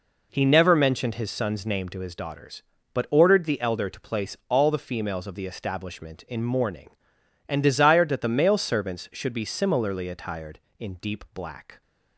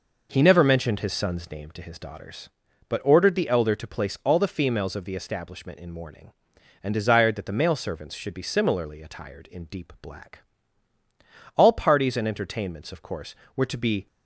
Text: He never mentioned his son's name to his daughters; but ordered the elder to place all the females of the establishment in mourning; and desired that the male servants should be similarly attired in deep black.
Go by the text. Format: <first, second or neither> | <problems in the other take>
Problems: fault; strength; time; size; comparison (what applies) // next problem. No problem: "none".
first | goes on to say "All parties and entertainments of course were to be"; strong; from 11.5 s on; 2.5 s long